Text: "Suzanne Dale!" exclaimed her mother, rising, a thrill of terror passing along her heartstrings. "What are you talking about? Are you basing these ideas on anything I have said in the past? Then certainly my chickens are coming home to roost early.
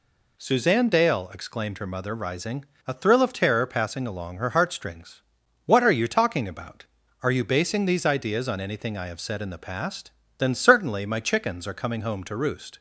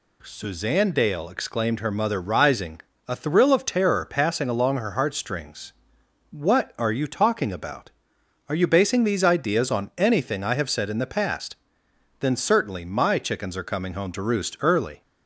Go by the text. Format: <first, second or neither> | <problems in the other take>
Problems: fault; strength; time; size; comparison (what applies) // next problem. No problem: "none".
second | stops before "early"; at 12.7 s